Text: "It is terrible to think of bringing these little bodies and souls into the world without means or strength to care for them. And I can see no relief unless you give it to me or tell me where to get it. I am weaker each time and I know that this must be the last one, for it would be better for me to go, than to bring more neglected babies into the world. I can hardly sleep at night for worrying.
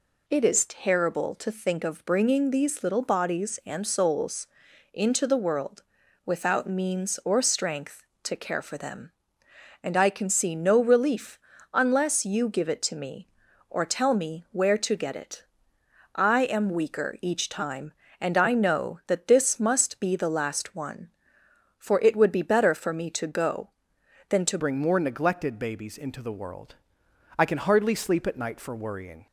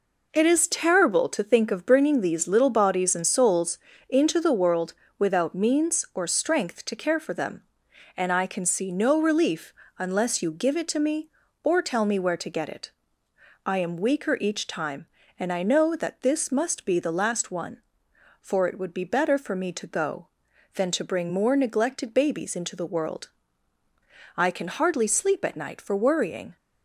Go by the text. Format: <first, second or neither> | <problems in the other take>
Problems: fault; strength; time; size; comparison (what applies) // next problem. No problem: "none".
second | pauses between "souls" and "into"; at 4.4 s; 0.44 s long; slight in the second // pauses between "world" and "without"; at 5.8 s; 0.42 s long; slight in the second // pauses between "relief" and "unless"; slight; at 11.3 s; 0.34 s long; slight in the second // changes voice at "bring"; from 24.5 s on; 4.7 s long